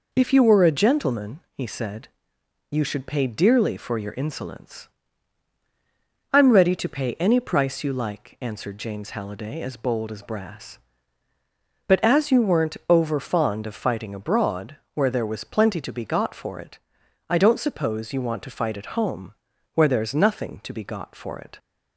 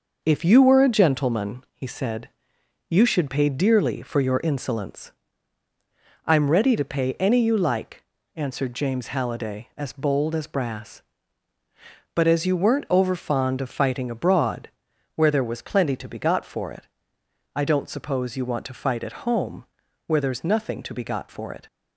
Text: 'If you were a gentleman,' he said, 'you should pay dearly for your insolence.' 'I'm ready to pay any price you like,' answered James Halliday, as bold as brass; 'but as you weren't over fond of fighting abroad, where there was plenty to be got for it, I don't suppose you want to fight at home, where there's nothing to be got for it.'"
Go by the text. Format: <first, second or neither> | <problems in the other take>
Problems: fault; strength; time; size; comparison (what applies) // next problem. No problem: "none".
first | skips "price"; at 7.4 s